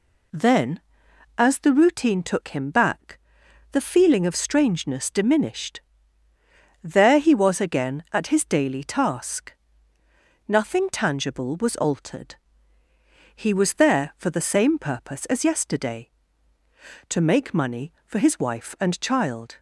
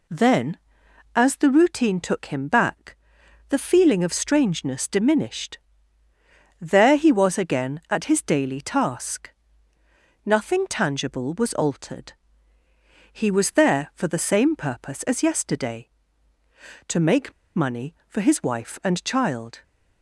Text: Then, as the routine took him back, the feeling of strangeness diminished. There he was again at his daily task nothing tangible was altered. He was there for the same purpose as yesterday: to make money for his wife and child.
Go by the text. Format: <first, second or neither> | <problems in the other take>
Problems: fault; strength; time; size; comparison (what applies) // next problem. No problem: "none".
first | pauses between "task" and "nothing"; noticeable; at 9.3 s; 0.94 s long; noticeable in the first // pauses between "make" and "money"; slight; at 17.3 s; 0.24 s long